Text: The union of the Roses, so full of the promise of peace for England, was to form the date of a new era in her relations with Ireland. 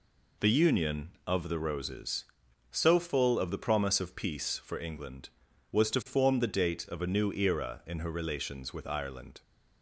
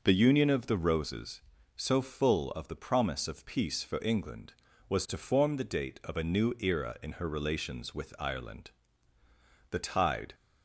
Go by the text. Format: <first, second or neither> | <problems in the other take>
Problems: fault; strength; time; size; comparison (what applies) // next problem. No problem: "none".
first | goes on to say "The tide"; noticeable; from 9.7 s on; 0.64 s long